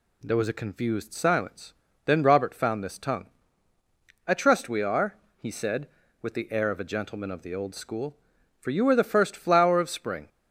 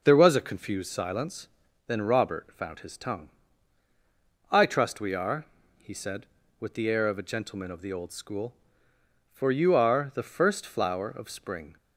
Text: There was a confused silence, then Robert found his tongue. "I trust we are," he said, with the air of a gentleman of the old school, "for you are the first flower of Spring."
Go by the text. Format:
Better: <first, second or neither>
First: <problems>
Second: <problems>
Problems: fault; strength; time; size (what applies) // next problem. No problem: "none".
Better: second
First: says "this" for "his"; at 2.8 s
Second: none